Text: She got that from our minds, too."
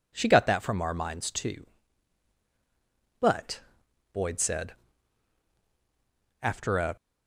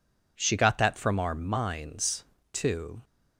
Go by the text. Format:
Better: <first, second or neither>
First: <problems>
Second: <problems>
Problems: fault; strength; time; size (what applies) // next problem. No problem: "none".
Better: second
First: goes on to say "But Boyd said After a"; strong; from 3.1 s on; 3.7 s long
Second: none